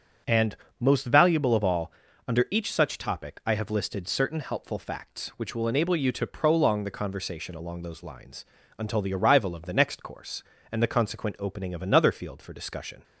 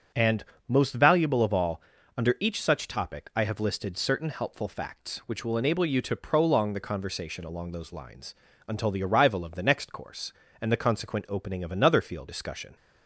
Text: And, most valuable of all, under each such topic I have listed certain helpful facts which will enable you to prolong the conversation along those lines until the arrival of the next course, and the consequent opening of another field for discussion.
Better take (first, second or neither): first